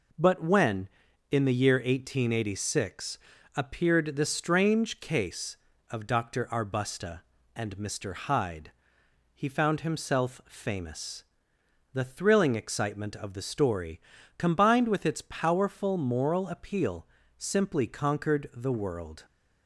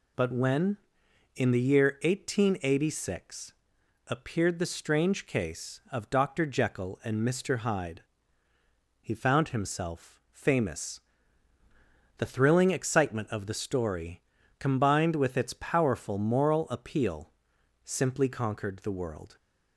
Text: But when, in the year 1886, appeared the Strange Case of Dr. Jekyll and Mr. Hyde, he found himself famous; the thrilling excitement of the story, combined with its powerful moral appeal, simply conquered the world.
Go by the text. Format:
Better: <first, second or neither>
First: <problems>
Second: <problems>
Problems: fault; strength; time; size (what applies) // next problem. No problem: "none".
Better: second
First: says "Arbusta" for "Jekyll"; at 6.5 s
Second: none